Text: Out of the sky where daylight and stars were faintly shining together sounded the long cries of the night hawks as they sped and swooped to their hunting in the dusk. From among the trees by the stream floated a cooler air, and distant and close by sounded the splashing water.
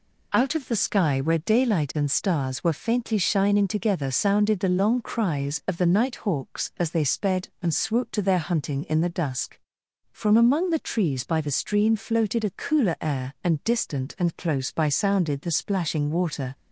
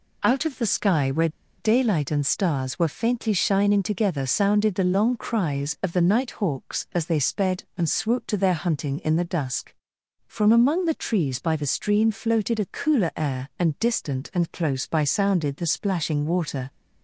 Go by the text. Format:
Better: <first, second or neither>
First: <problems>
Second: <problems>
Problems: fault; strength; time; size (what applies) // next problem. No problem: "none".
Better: first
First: none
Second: pauses between "where" and "daylight"; slight; at 1.2 s; 0.30 s long